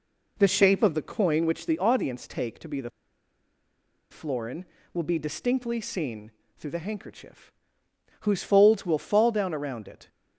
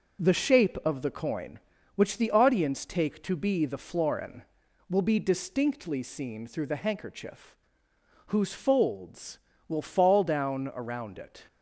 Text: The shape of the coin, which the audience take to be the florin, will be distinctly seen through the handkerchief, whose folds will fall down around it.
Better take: second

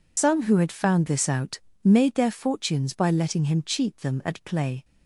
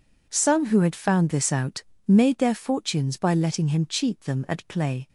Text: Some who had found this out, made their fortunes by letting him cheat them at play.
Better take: second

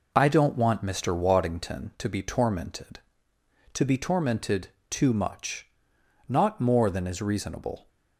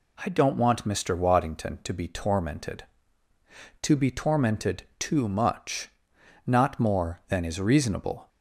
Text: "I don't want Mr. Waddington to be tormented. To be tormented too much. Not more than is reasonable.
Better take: neither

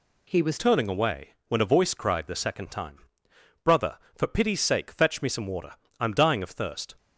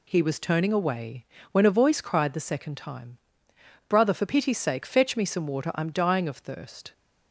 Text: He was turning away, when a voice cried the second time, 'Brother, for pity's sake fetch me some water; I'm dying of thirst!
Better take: second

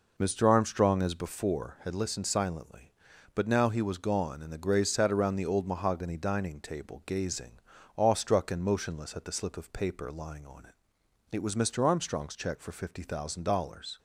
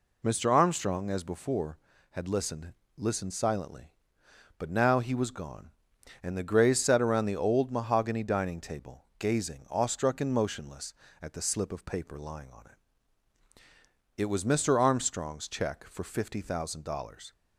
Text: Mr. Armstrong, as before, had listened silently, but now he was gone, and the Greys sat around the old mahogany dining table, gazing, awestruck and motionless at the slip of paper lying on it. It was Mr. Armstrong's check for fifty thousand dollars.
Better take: first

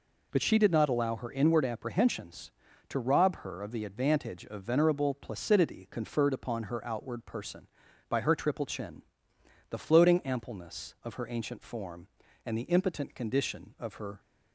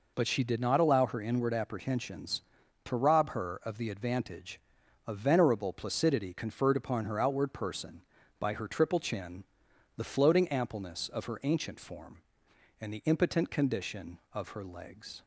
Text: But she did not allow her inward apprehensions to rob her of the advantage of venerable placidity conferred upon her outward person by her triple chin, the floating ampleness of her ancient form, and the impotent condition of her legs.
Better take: second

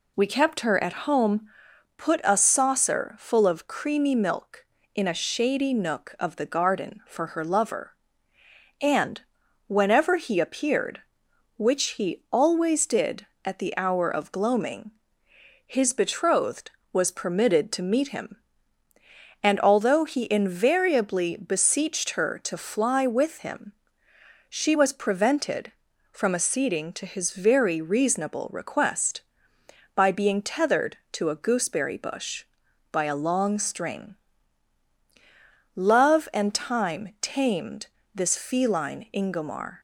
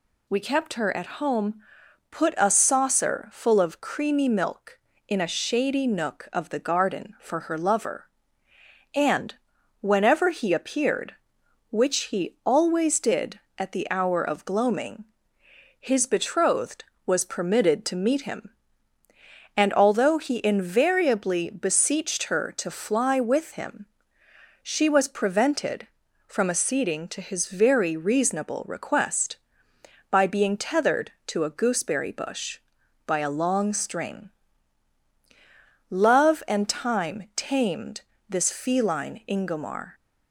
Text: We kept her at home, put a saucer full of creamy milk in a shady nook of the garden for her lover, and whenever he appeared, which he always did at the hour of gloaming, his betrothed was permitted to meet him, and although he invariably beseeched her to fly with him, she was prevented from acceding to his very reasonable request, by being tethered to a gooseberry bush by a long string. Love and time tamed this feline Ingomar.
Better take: second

